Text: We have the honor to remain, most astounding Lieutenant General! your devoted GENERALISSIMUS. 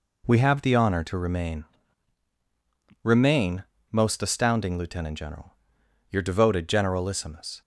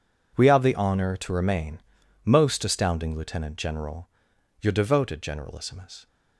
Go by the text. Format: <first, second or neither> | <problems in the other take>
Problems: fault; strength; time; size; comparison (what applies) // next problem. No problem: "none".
second | says "remain" twice; at 3.0 s